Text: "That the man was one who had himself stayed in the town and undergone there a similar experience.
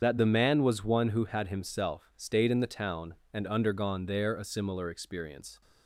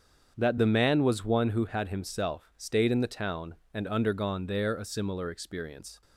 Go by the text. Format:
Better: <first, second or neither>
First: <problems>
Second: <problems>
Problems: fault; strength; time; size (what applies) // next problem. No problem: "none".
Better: second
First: loses the start of "That"; at 0.0 s; 60 ms // starts louder than the rest; strong; until 1.0 s; 7.5 dB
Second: starts louder than the rest; strong; until 1.3 s; 7.5 dB